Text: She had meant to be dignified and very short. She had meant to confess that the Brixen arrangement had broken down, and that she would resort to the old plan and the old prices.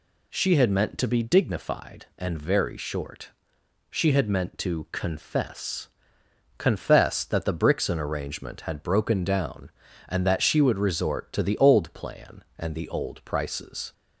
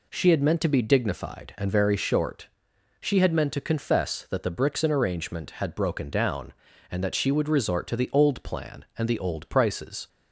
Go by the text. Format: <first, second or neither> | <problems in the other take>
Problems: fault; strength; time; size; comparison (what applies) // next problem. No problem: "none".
second | says "confess" twice; at 6.5 s